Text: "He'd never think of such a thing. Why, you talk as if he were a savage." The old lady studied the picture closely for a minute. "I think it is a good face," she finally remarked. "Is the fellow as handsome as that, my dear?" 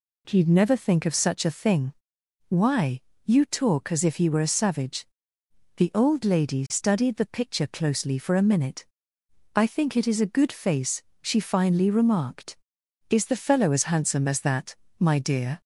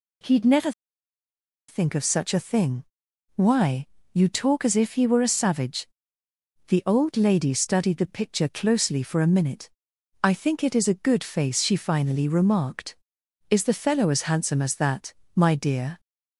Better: first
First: none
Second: pauses between "never" and "think"; noticeable; at 0.7 s; 0.97 s long

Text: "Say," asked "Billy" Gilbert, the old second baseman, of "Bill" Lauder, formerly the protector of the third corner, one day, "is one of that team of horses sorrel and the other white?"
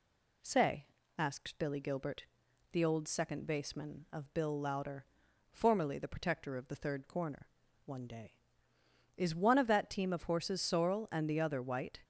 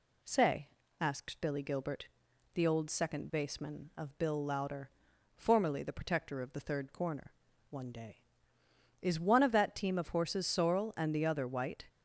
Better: neither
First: none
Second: none

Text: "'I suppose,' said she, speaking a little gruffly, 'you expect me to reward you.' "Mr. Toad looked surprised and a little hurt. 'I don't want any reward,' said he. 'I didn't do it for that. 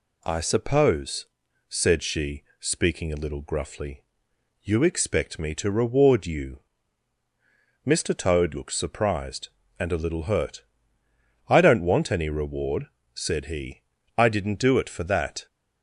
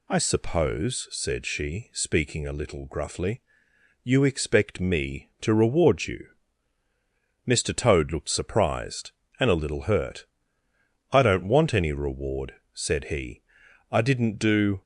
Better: first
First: none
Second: stops before "it for that"; at 14.8 s

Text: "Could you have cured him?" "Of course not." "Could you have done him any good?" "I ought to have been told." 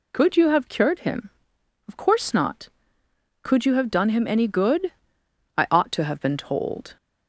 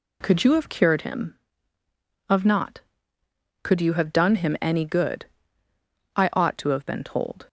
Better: first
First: none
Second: skips "course"; at 2.4 s

